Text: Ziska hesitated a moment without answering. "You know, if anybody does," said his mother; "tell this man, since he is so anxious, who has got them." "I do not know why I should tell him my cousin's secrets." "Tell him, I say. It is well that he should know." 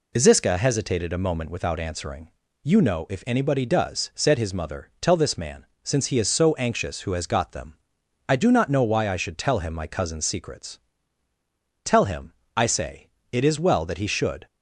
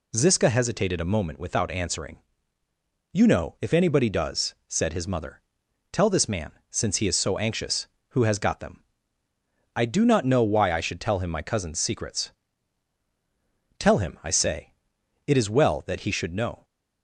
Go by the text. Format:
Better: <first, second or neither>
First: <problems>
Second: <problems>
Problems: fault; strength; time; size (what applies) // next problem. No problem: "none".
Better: second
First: stops before "know"; at 14.4 s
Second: none